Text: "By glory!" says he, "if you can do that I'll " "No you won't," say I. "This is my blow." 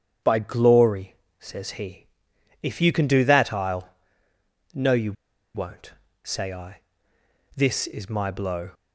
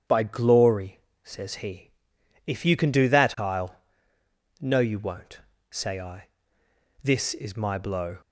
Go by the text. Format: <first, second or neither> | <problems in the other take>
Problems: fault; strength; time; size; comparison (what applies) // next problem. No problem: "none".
second | starts louder than the rest; strong; until 1.4 s; 8 dB; strong in the second // pauses between "you" and "won't"; at 5.1 s; 0.41 s long